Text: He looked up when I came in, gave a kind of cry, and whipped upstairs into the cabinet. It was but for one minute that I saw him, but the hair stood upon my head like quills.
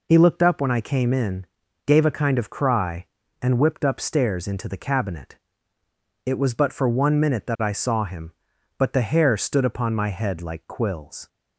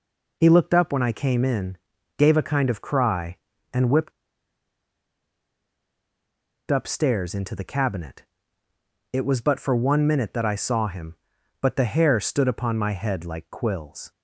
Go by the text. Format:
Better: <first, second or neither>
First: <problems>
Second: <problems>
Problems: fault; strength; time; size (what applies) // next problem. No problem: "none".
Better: first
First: none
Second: pauses between "whipped" and "upstairs"; strong; at 4.1 s; 2.5 s long